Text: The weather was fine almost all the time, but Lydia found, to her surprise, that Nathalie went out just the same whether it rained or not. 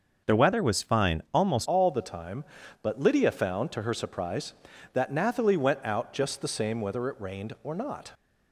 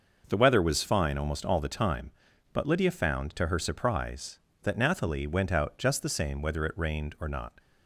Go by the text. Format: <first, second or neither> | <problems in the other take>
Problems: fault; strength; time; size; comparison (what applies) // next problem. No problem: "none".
second | starts louder than the rest; until 1.4 s; 6 dB // changes voice at "all"; from 1.6 s on; 6.5 s long